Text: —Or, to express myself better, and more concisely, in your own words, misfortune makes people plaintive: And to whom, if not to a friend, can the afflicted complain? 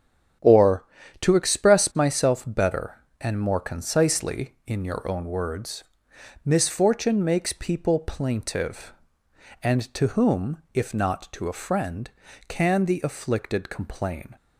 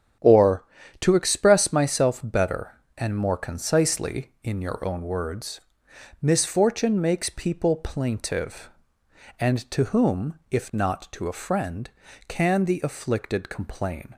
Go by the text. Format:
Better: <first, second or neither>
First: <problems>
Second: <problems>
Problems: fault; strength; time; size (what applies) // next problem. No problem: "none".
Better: neither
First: starts louder than the rest; strong; until 1.7 s; 9.5 dB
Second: starts louder than the rest; strong; until 1.5 s; 9 dB